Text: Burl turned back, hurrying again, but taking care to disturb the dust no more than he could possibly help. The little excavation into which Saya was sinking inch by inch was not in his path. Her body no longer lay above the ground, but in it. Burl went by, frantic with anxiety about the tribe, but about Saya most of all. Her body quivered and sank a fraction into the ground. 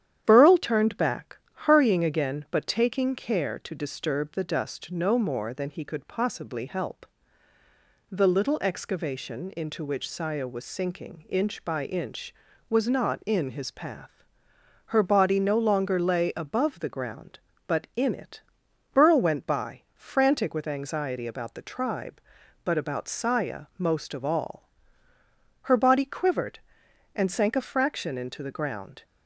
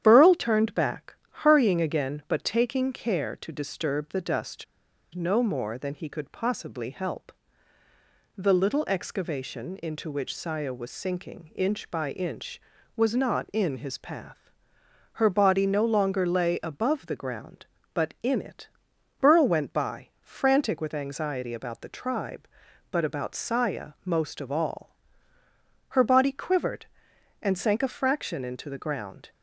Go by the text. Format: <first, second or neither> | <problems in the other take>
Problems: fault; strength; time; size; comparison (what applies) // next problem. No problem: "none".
first | starts louder than the rest; strong; until 1.0 s; 10 dB; strong in the first // pauses between "dust" and "no"; noticeable; at 4.6 s; 0.49 s long